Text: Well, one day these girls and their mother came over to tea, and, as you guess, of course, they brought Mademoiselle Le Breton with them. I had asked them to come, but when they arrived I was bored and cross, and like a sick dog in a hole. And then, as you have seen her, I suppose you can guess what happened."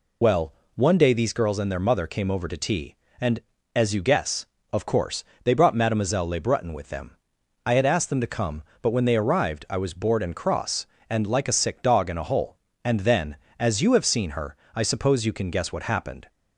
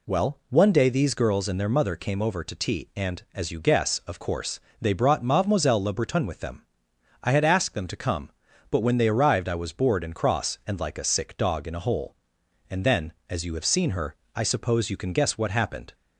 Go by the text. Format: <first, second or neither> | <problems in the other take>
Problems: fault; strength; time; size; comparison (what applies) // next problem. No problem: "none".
second | loses the start of "Well"; at 0.2 s; 45 ms